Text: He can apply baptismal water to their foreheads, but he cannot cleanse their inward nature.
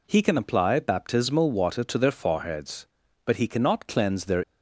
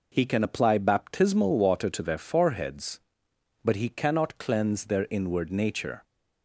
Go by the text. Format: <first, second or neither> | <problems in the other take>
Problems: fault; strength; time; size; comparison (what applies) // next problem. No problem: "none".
second | stops before "inward nature"; at 4.4 s